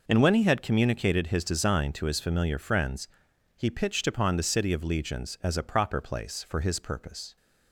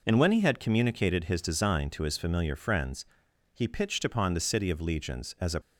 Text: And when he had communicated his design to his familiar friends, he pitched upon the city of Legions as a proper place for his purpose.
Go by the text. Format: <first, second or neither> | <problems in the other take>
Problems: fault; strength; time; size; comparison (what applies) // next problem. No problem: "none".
first | stops before "proper place for his purpose"; at 5.6 s